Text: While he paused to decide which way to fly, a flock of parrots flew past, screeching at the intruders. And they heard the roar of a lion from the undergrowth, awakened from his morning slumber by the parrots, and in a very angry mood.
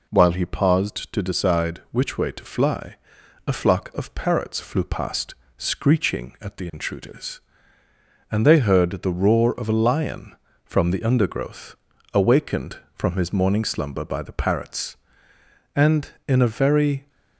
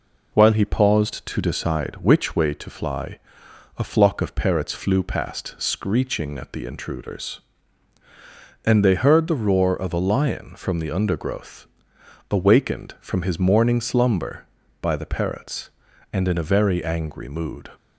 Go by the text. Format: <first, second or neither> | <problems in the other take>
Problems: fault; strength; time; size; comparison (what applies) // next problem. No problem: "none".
second | stops before "angry mood"; at 17.0 s